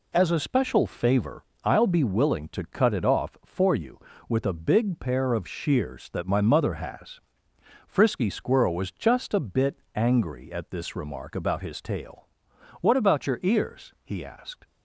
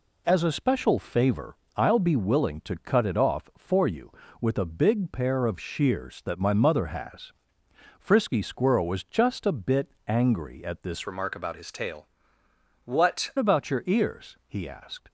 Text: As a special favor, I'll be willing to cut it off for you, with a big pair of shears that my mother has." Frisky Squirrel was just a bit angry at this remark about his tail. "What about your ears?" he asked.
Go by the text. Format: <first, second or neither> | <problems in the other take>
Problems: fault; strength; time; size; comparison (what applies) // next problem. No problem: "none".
first | pauses between "bit" and "angry"; slight; at 9.9 s; 0.16 s long; slight in the first // changes voice from "remark" to "What"; from 11.0 to 13.3 s; 2.3 s long